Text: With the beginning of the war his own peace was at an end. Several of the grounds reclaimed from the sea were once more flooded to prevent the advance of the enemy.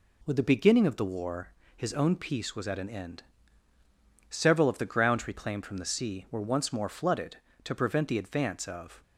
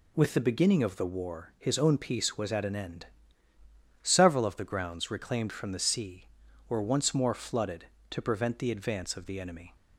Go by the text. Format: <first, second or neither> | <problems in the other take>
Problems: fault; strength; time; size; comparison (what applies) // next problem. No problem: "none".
second | pauses between "war" and "his"; slight; at 1.4 s; 0.28 s long // stops before "the enemy"; at 9.0 s